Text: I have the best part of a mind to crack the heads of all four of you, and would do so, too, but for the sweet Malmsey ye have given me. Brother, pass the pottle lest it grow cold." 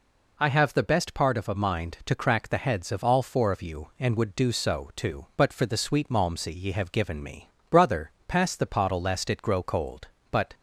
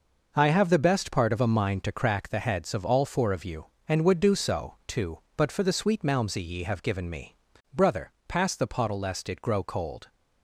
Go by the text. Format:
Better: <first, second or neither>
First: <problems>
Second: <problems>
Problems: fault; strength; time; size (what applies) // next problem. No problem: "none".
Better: second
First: goes on to say "But"; slight; from 10.2 s on; 0.24 s long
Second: none